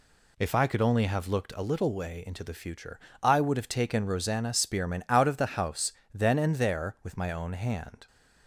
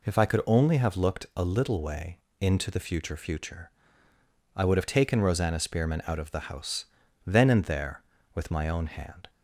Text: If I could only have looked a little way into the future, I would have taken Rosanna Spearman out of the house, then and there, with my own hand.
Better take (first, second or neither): first